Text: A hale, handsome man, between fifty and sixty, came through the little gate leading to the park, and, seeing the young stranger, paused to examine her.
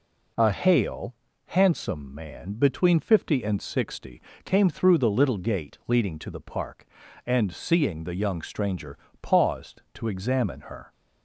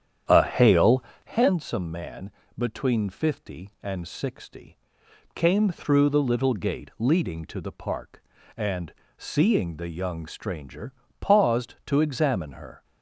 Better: first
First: none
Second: starts louder than the rest; strong; until 1.4 s; 9 dB

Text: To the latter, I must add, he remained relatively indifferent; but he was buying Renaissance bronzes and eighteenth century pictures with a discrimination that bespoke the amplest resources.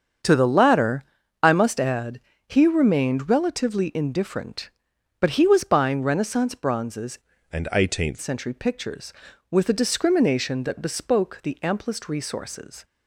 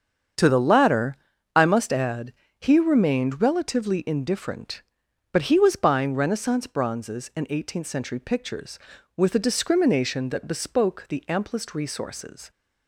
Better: second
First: starts louder than the rest; strong; until 1.6 s; 7.5 dB // changes voice from "and" to "eighteenth"; from 7.5 to 8.1 s; 0.6 s long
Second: starts louder than the rest; strong; until 1.7 s; 7.5 dB

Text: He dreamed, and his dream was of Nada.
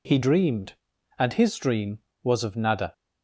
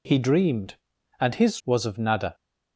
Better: first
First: none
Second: skips "dream"; at 1.6 s

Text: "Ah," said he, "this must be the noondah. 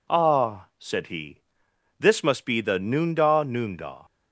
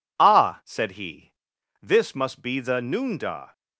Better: second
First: says "noondah" twice; at 3.4 s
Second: none

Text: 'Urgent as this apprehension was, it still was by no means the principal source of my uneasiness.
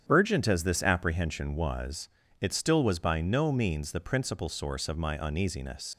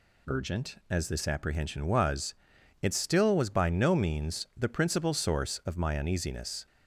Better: second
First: starts louder than the rest; strong; until 1.0 s; 9 dB // leaves "uneasiness" unfinished; at 5.9 s; 90 ms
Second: none

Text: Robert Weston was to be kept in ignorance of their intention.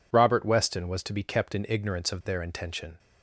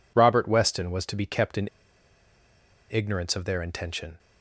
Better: first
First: none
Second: pauses between "in" and "ignorance"; at 1.6 s; 1.2 s long

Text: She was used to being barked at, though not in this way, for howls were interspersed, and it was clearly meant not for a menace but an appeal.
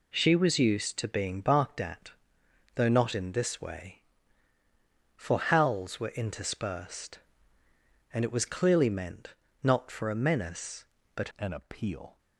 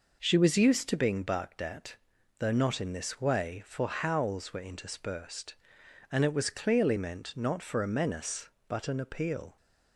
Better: second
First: pauses between "meant" and "not"; slight; at 9.3 s; 0.30 s long // changes voice at "an"; from 11.3 s on; 0.8 s long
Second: none

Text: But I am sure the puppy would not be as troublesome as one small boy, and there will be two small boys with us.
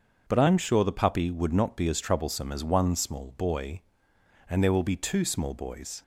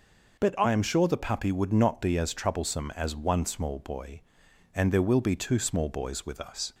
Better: second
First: starts louder than the rest; until 1.2 s; 6.5 dB // stops before "with us"; at 6.0 s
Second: none

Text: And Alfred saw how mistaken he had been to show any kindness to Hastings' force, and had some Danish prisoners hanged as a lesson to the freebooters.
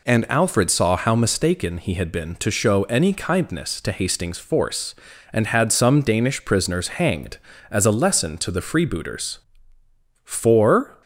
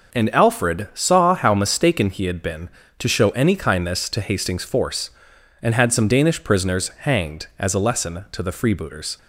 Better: second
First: goes on to say "For"; noticeable; from 10.2 s on; 0.78 s long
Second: none

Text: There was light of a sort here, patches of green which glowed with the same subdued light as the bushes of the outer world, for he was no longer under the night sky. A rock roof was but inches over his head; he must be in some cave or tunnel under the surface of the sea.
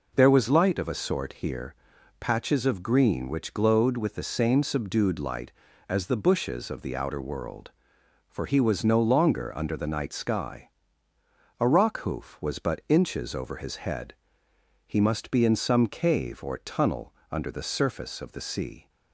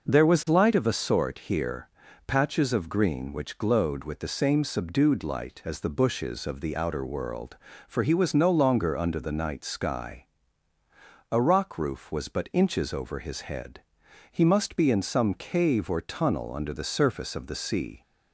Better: second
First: says "hoof" for "roof"; at 11.9 s // pauses between "tunnel" and "under"; slight; at 17.1 s; 0.20 s long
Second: none

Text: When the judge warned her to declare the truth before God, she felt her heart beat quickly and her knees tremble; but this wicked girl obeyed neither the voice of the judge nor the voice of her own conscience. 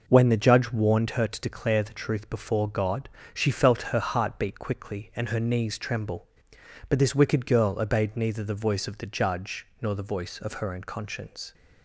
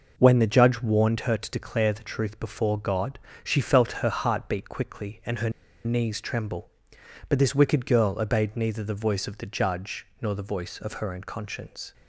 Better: first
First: none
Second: pauses between "her" and "knees"; slight; at 5.5 s; 0.34 s long

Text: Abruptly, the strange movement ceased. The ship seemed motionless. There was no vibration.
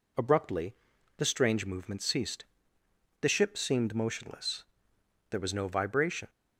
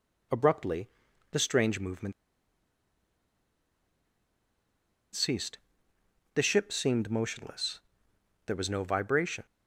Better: first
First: none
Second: pauses between "movement" and "ceased"; strong; at 2.1 s; 3.0 s long

